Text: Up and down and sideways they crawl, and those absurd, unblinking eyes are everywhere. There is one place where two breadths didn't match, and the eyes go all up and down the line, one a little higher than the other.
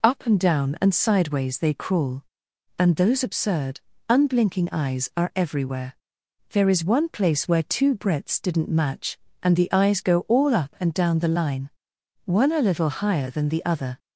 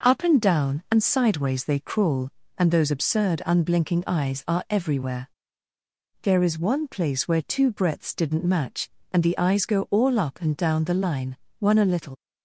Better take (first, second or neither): first